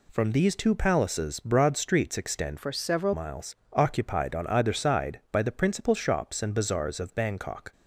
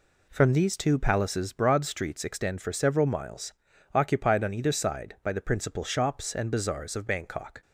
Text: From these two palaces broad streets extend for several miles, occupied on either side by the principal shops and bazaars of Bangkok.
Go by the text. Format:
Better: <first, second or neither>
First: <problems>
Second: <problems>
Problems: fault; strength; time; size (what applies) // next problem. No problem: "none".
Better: second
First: changes voice from "for" to "several"; from 2.5 to 3.1 s; 0.6 s long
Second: none